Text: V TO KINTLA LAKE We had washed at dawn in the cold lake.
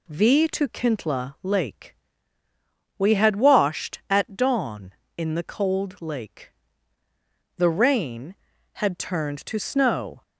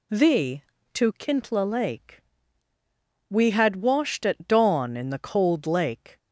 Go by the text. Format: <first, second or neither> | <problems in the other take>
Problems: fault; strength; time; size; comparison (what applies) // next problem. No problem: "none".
second | pauses between "LAKE" and "We"; at 1.9 s; 1.0 s long; also in the second // goes on to say "The rain had turned to snow"; strong; from 7.5 s on; 2.6 s long